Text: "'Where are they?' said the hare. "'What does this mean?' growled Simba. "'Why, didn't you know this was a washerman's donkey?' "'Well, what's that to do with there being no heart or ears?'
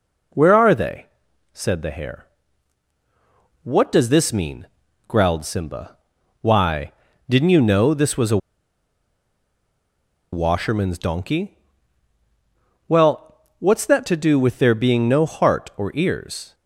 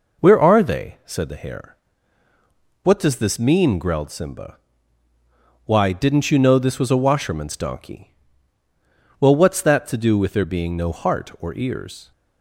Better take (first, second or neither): second